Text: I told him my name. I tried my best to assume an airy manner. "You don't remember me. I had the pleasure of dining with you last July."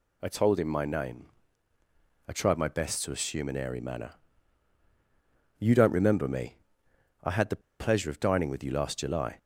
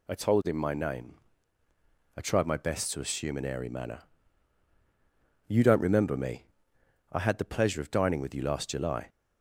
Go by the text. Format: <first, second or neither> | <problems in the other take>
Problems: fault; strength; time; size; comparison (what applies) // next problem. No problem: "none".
second | pauses between "the" and "pleasure"; slight; at 7.6 s; 0.20 s long